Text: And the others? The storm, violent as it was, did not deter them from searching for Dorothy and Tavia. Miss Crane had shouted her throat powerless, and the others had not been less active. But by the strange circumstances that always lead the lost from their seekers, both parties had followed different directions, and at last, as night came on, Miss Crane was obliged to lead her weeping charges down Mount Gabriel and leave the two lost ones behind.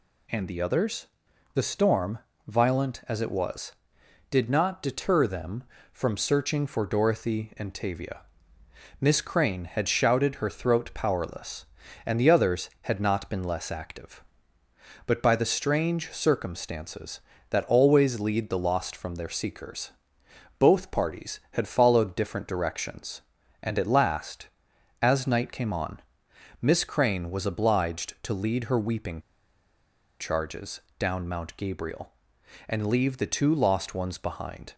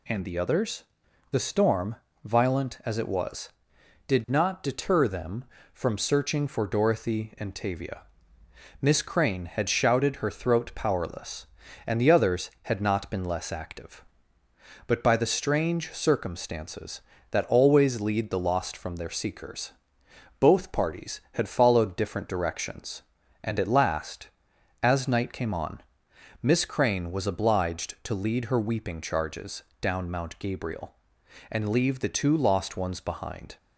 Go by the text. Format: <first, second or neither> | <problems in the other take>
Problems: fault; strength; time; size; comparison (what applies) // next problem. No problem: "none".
second | pauses between "weeping" and "charges"; at 29.1 s; 1.0 s long // pauses between "charges" and "down"; slight; at 30.8 s; 0.18 s long; slight in the second